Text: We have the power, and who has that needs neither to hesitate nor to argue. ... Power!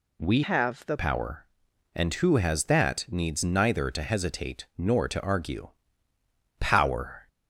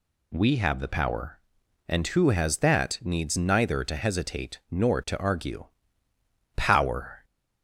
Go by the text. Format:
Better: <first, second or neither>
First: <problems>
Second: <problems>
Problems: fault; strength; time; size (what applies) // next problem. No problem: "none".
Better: second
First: changes voice from "have" to "the"; from 0.4 to 0.9 s; 0.5 s long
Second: none